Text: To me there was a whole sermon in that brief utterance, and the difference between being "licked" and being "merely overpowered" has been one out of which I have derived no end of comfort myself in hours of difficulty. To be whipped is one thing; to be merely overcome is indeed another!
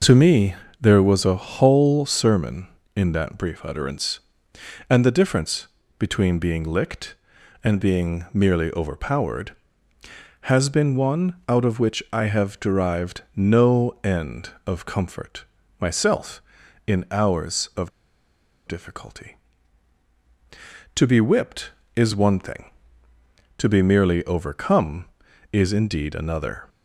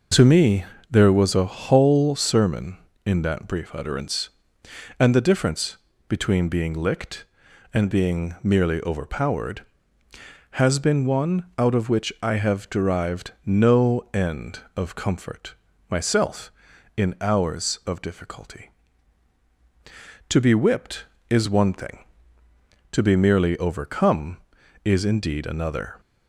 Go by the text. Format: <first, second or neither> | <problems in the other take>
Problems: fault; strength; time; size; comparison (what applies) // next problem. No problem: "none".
second | pauses between "me" and "there"; slight; at 0.5 s; 0.26 s long; slight in the second // pauses between "difference" and "between"; slight; at 5.6 s; 0.28 s long; slight in the second // pauses between "derived" and "no"; slight; at 13.2 s; 0.16 s long; slight in the second // pauses between "comfort" and "myself"; slight; at 15.4 s; 0.34 s long; slight in the second // pauses between "of" and "difficulty"; noticeable; at 17.9 s; 0.78 s long